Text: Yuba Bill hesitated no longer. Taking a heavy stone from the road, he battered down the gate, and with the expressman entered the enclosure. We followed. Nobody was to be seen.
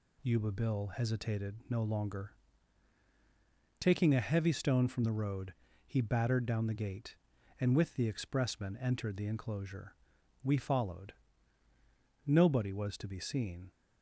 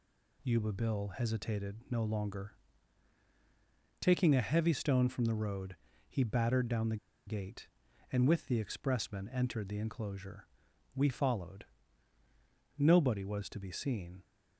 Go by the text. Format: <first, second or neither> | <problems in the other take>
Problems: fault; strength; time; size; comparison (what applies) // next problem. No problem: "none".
first | pauses between "the" and "gate"; slight; at 6.9 s; 0.30 s long